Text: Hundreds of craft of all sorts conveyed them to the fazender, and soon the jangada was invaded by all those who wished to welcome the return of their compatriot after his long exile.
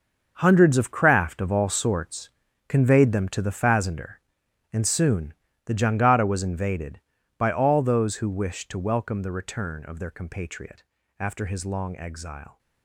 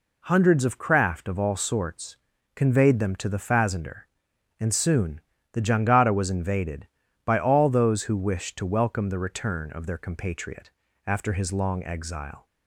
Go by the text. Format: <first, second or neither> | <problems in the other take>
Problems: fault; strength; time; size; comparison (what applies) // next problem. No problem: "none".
second | gets quieter; strong; throughout; 12 dB // pauses between "sorts" and "conveyed"; at 2.2 s; 0.38 s long; also in the second // pauses between "soon" and "the"; slight; at 5.3 s; 0.34 s long; slight in the second // pauses between "compatriot" and "after"; at 10.8 s; 0.38 s long; also in the second